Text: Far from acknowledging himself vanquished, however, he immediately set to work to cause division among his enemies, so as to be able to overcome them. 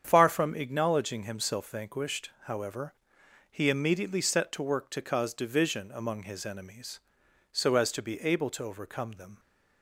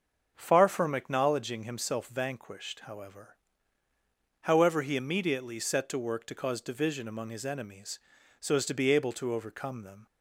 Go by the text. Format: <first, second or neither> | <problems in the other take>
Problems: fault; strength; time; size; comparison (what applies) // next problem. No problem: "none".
first | starts louder than the rest; until 1.3 s; 6.5 dB; strong in the first // says "however" twice; at 4.4 s